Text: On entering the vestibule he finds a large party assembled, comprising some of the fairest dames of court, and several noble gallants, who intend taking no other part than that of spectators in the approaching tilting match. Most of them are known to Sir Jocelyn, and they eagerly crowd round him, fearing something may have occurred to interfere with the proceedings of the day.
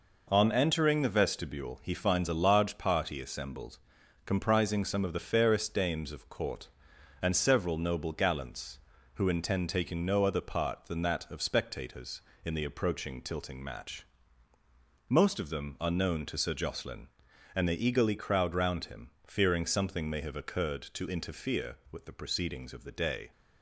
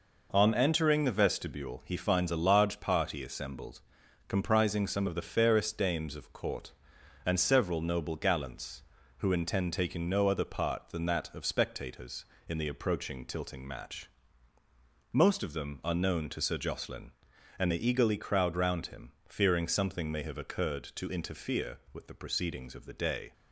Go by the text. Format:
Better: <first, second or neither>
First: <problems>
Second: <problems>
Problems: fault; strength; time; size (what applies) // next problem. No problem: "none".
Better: neither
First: none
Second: none